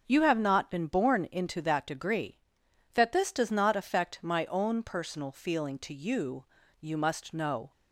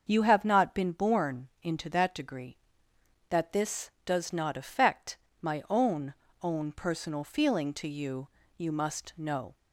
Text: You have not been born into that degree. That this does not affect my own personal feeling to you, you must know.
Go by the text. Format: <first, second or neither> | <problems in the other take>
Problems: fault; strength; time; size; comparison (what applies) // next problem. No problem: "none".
first | starts louder than the rest; until 1.0 s; 6.5 dB; also in the first // pauses between "affect" and "my"; slight; at 5.1 s; 0.24 s long // says "own" twice; at 6.4 s